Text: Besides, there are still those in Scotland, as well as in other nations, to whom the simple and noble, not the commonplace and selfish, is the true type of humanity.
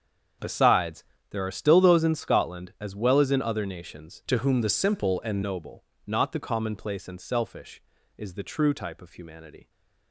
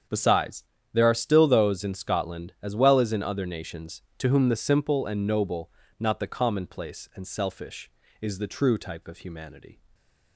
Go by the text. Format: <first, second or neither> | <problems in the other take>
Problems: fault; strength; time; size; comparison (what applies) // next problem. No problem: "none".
second | starts louder than the rest; until 1.6 s; 7 dB; strong in the second // changes voice from "to" to "and"; from 4.2 to 5.4 s; 1.2 s long